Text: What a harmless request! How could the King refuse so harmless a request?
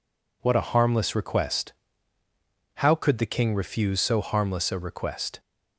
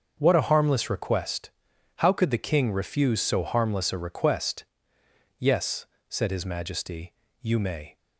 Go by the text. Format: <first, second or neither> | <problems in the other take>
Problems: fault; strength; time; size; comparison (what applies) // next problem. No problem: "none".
first | starts louder than the rest; until 1.1 s; 6.5 dB // goes on to say "Yes said his Majesty you may"; strong; from 5.3 s on; 2.5 s long